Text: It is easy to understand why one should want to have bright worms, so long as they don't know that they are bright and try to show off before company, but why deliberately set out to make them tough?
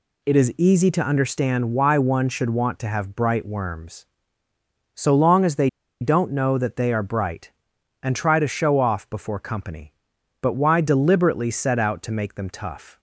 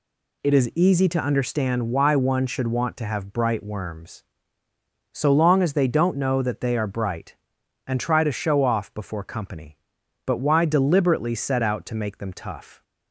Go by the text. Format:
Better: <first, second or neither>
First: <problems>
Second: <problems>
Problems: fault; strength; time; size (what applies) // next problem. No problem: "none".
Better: second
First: pauses between "they" and "don't"; slight; at 5.6 s; 0.33 s long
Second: none